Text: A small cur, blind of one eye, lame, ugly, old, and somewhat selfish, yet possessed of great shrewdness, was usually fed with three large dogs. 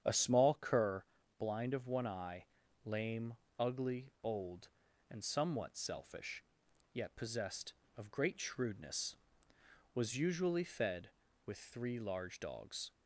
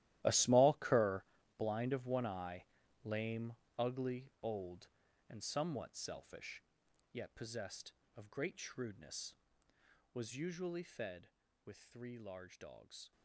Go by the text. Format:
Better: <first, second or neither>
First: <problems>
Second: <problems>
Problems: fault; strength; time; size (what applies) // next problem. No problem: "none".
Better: first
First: starts louder than the rest; strong; until 1.4 s; 8.5 dB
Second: gets quieter; strong; throughout; 16.5 dB // starts louder than the rest; strong; until 1.5 s; 14.5 dB